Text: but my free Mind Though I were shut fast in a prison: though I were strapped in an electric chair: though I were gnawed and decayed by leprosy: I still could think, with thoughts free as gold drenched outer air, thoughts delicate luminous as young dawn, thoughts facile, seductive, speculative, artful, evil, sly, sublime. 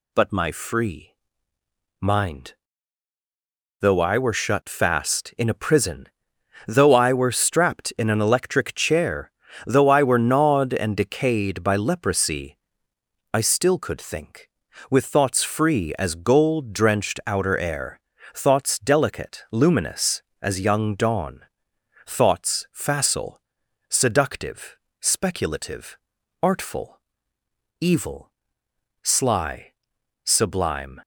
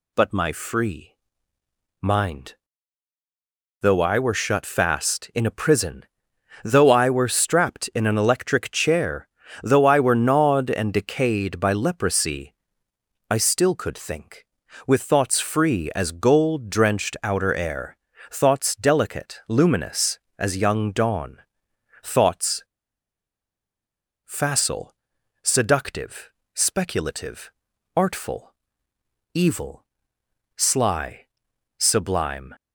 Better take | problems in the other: first | pauses between "free" and "Mind"; noticeable; at 1.1 s; 0.86 s long; noticeable in the first // pauses between "Mind" and "Though"; strong; at 2.5 s; 1.2 s long; strong in the first // pauses between "thoughts" and "facile"; strong; at 22.6 s; 1.6 s long

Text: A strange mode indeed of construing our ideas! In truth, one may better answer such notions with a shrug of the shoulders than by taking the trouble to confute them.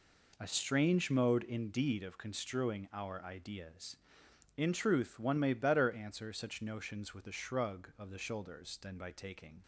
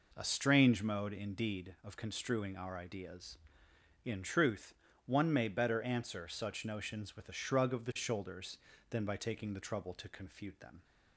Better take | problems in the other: second | stops before "the trouble to confute them"; at 9.6 s

